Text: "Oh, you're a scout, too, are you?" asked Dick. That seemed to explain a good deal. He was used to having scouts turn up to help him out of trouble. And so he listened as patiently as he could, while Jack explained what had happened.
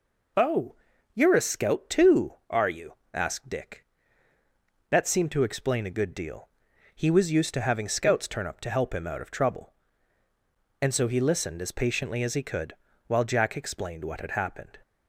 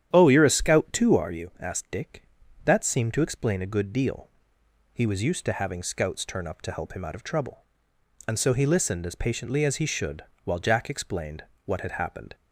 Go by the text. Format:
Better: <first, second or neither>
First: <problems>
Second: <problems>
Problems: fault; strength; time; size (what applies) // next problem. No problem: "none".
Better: first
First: none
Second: starts louder than the rest; strong; until 1.1 s; 10 dB // says "should" for "could"; at 9.8 s // pauses between "explained" and "what"; slight; at 11.4 s; 0.20 s long